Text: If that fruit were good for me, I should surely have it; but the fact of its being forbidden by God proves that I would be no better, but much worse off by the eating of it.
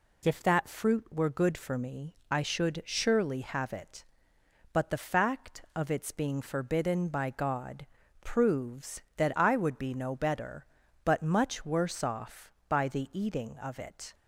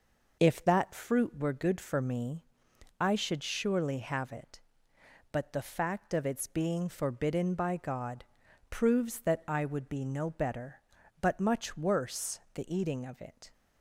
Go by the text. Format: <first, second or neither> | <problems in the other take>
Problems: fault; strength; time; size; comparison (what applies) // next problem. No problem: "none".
first | pauses between "God" and "proves"; noticeable; at 8.2 s; 0.46 s long; slight in the first // skips "off by"; at 12.4 s